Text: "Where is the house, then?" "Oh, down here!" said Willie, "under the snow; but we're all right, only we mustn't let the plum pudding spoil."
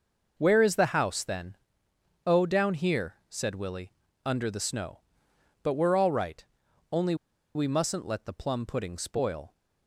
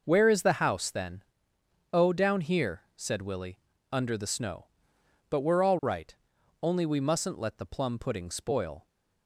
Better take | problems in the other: second | pauses between "only" and "we"; at 7.1 s; 0.40 s long

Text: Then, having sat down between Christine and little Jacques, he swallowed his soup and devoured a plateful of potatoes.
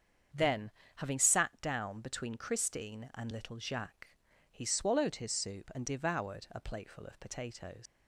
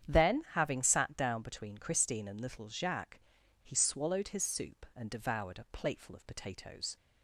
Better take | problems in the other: second | starts louder than the rest; strong; until 1.6 s; 7.5 dB; strong in the second // leaves "potatoes" unfinished; at 7.8 s; 105 ms

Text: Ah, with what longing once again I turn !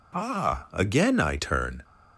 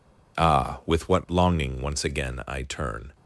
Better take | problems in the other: second | skips "with what longing once"; at 0.7 s

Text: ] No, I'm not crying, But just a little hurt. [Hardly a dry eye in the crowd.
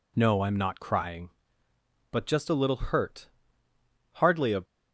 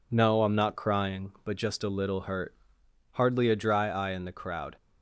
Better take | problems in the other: second | stops before "dry eye in the crowd"; at 4.6 s

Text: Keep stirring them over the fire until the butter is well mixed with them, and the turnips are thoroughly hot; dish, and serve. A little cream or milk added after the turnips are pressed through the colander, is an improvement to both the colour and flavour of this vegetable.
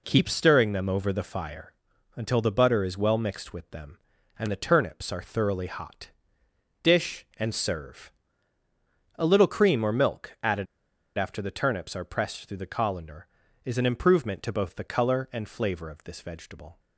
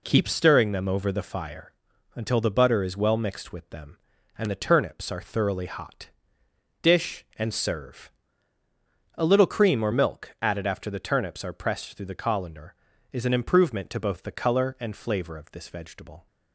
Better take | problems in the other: second | pauses between "fire" and "until"; at 1.7 s; 0.42 s long; also in the second // pauses between "added" and "after"; noticeable; at 10.6 s; 0.53 s long

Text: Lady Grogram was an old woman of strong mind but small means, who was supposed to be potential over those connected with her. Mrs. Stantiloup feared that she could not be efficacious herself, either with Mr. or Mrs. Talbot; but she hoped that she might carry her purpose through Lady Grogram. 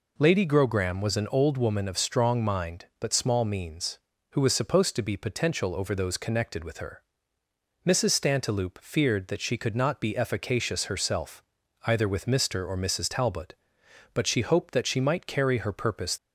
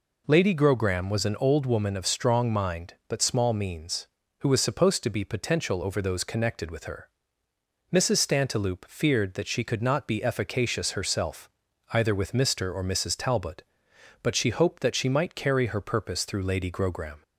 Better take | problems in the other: second | stops before "through Lady Grogram"; at 16.1 s

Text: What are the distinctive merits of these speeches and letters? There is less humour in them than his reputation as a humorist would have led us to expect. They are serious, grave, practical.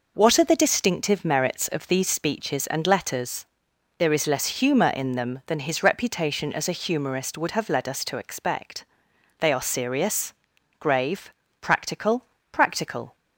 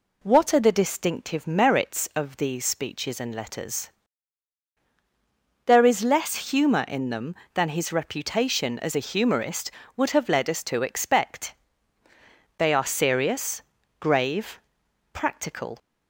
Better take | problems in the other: second | says "practical" twice; at 12.5 s

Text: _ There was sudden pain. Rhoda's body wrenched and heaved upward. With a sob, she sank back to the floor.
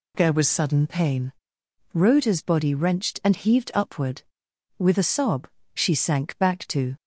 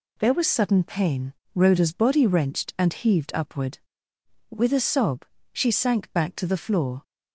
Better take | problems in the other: second | stops before "the floor"; at 6.9 s

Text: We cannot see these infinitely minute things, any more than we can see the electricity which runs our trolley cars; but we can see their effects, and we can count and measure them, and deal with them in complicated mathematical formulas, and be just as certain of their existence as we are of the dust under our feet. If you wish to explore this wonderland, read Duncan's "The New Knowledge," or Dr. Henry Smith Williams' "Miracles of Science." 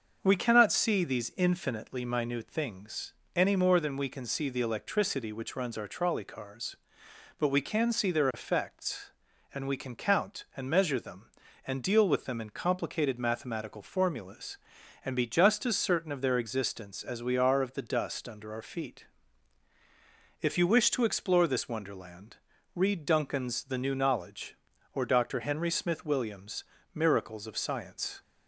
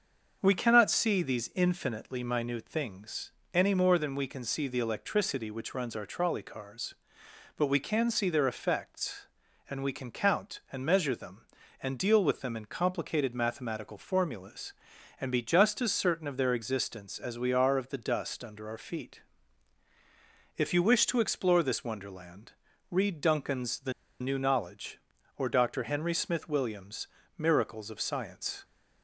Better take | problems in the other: first | starts louder than the rest; until 1.4 s; 6.5 dB; also in the first // pauses between "The" and "New"; slight; at 23.9 s; 0.27 s long // pauses between "Williams" and "Miracles"; slight; at 27.0 s; 0.32 s long; slight in the first

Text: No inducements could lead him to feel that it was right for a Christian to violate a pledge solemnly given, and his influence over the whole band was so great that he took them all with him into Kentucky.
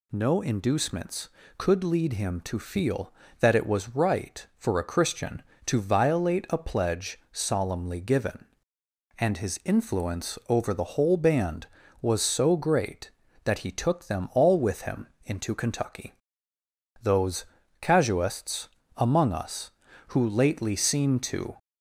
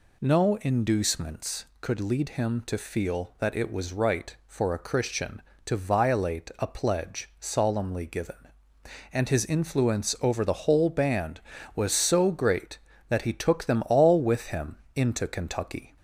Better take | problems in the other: second | pauses between "him" and "into"; slight; at 15.0 s; 0.16 s long; slight in the second // goes on to say "Those casuists among us who lately seem to"; strong; from 17.0 s on; 4.5 s long

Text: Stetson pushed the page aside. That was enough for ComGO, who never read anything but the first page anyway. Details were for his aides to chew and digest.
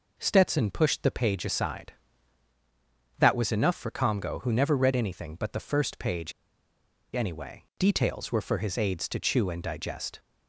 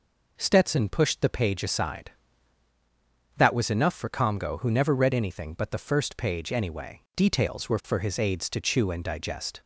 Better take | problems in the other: second | pauses between "page" and "anyway"; noticeable; at 6.3 s; 0.83 s long

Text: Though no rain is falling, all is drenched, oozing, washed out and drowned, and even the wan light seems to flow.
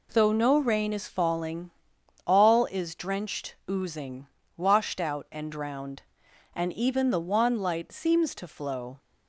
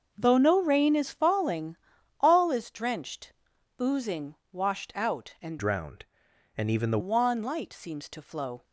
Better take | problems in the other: first | starts louder than the rest; noticeable; until 1.1 s; 6 dB // changes voice from "drowned" to "the"; from 5.5 to 6.9 s; 1.4 s long

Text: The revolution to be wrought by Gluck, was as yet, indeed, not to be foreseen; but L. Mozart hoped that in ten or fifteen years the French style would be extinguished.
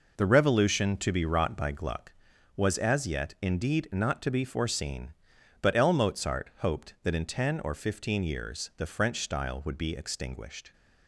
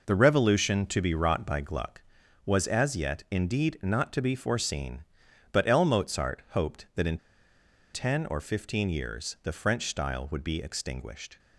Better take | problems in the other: first | pauses between "in" and "ten"; noticeable; at 7.1 s; 0.77 s long

